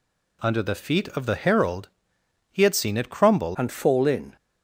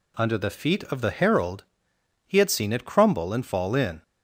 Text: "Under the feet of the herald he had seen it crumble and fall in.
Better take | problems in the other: second | pauses between "herald" and "he"; noticeable; at 1.8 s; 0.62 s long; noticeable in the second // changes voice at "and"; from 3.5 s on; 0.8 s long

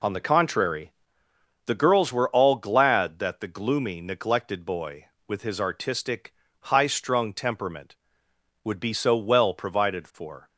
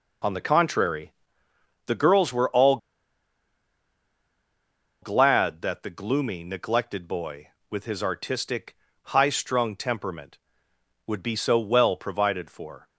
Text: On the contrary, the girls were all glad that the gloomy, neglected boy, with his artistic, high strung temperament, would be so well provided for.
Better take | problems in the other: first | pauses between "all" and "glad"; strong; at 2.7 s; 2.2 s long

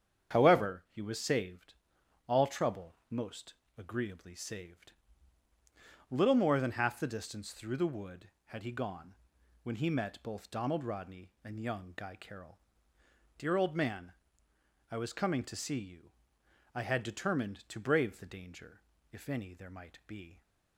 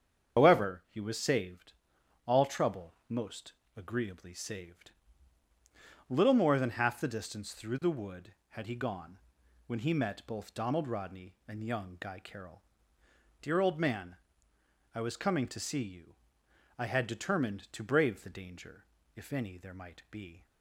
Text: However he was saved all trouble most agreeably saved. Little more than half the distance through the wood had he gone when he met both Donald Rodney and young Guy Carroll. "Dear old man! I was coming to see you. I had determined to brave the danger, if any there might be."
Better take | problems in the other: first | loses the start of "However"; at 0.3 s; 70 ms // starts louder than the rest; strong; until 1.4 s; 7.5 dB; strong in the first // pauses between "saved" and "all"; noticeable; at 1.7 s; 0.52 s long; noticeable in the first // pauses between "most" and "agreeably"; slight; at 3.5 s; 0.26 s long; slight in the first // pauses between "gone" and "when"; noticeable; at 9.1 s; 0.48 s long; noticeable in the first

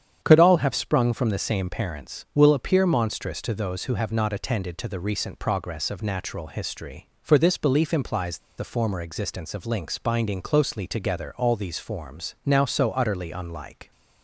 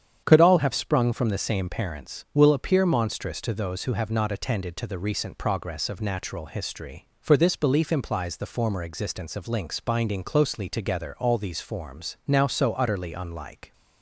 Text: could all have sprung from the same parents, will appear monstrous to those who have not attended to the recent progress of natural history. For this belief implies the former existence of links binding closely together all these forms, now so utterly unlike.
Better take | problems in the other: second | starts louder than the rest; strong; until 1.2 s; 8.5 dB; strong in the second // pauses between "implies" and "the"; slight; at 8.3 s; 0.19 s long

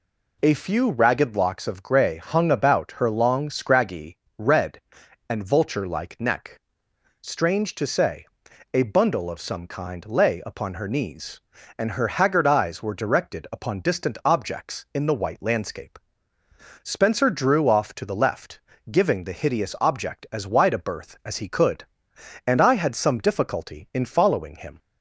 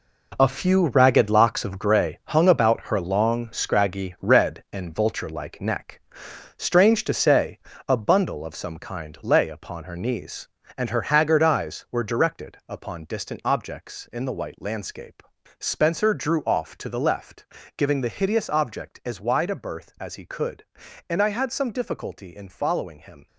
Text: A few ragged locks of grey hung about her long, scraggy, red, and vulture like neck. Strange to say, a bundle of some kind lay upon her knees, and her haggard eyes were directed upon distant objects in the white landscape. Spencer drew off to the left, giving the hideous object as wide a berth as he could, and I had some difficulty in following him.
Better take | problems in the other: first | gets quieter; strong; throughout; 10 dB

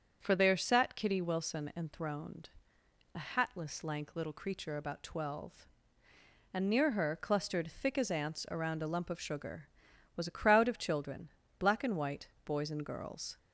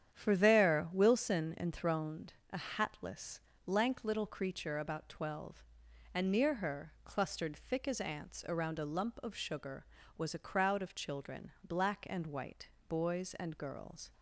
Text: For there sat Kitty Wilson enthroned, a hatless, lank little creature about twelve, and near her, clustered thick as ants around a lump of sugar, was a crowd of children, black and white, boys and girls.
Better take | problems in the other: first | starts louder than the rest; strong; until 1.1 s; 9 dB; strong in the first // skips "sat Kitty"; at 0.9 s

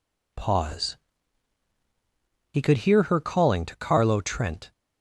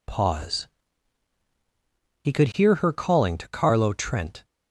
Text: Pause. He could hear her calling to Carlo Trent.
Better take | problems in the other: neither | none

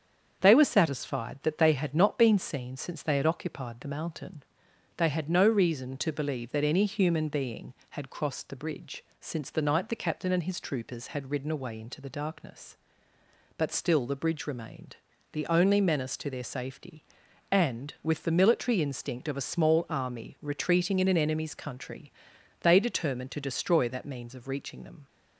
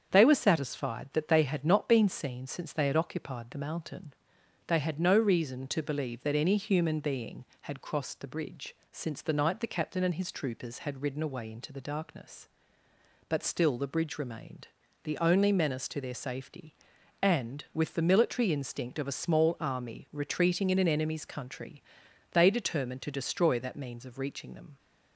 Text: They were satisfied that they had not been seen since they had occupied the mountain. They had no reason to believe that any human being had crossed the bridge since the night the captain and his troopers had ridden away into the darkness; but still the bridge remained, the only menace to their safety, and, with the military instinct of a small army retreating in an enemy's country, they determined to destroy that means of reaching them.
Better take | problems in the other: neither | starts louder than the rest; strong; the same in both // pauses between "bridge" and "since"; slight; the same in both

